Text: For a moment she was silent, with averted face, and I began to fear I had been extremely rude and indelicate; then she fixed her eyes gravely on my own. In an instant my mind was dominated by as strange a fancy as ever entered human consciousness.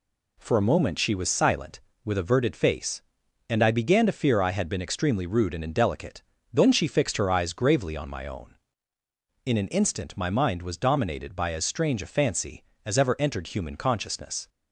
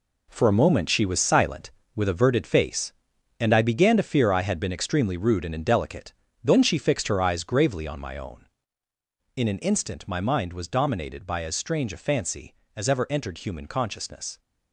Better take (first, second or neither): first